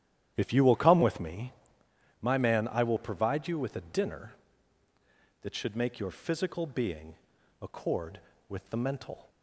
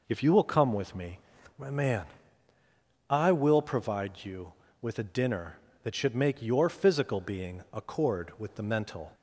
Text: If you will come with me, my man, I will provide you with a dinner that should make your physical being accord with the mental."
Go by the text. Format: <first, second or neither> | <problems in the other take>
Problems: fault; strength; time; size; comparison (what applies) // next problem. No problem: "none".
second | starts louder than the rest; strong; until 1.9 s; 11 dB // pauses between "being" and "accord"; noticeable; at 7.1 s; 0.46 s long